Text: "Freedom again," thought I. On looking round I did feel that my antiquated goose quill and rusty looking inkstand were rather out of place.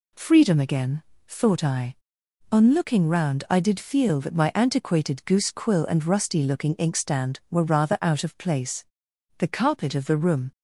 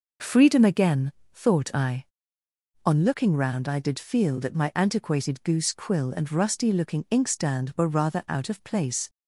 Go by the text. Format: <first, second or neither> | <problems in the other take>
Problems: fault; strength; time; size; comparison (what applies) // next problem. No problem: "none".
second | goes on to say "The carpet of the room"; noticeable; from 9.3 s on; 1.1 s long